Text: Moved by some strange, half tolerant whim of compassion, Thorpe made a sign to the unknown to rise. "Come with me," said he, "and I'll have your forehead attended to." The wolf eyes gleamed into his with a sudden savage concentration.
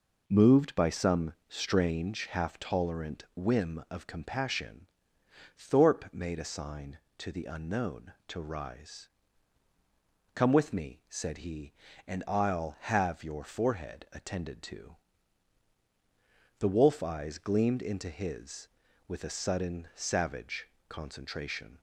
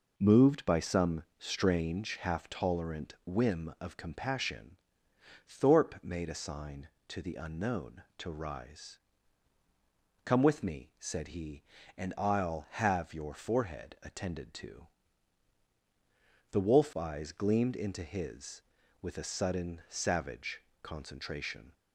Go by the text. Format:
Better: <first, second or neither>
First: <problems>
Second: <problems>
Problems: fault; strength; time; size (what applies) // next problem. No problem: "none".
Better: neither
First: pauses between "savage" and "concentration"; slight; at 20.6 s; 0.20 s long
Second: pauses between "savage" and "concentration"; slight; at 20.6 s; 0.20 s long